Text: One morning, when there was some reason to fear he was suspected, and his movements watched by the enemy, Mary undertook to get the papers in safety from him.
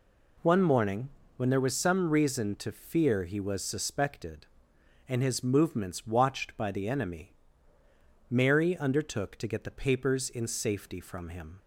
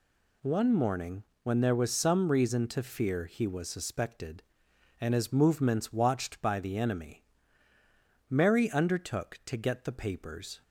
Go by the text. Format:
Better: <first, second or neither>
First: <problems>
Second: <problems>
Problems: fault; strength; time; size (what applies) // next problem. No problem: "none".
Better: first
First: none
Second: stops before "in safety from him"; at 10.6 s